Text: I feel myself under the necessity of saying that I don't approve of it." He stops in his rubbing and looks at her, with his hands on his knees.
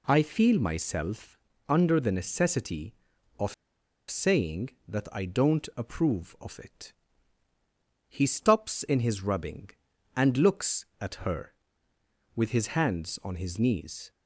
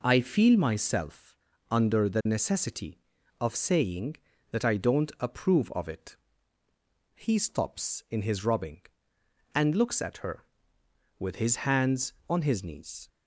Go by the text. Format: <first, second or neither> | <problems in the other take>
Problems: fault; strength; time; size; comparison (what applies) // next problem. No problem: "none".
second | pauses between "myself" and "under"; slight; at 1.3 s; 0.28 s long; slight in the second // pauses between "of" and "saying"; noticeable; at 3.5 s; 0.55 s long